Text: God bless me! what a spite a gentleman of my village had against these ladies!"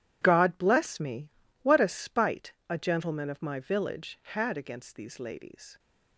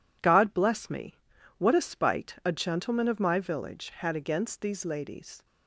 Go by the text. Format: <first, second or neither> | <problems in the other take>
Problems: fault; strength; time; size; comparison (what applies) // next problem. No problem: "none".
second | gets quieter; strong; throughout; 13.5 dB // pauses between "spite" and "a"; slight; at 2.5 s; 0.16 s long